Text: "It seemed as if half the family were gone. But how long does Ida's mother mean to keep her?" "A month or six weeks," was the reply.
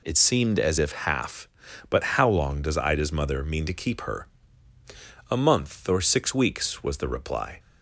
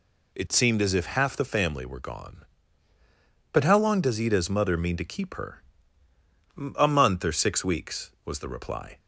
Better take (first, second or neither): second